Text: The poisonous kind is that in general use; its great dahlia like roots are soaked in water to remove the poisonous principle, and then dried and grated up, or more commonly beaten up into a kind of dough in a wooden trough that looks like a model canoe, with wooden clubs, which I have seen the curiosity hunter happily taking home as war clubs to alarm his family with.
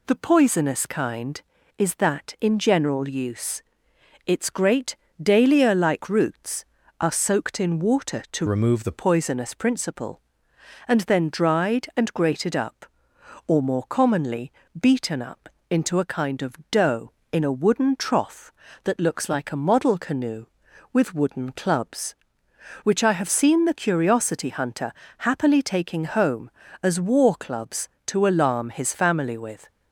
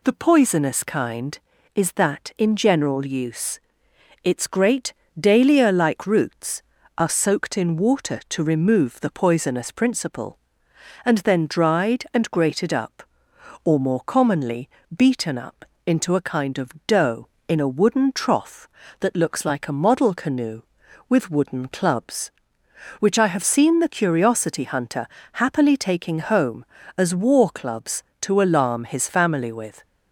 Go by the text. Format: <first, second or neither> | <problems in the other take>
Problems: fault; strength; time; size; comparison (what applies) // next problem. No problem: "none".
second | pauses between "great" and "dahlia"; slight; at 4.9 s; 0.22 s long; slight in the second // changes voice from "remove" to "the"; from 8.4 to 8.9 s; 0.5 s long // pauses between "commonly" and "beaten"; slight; at 14.5 s; 0.30 s long; slight in the second // pauses between "up" and "into"; slight; at 15.4 s; 0.20 s long; slight in the second // pauses between "hunter" and "happily"; slight; at 24.9 s; 0.26 s long; slight in the second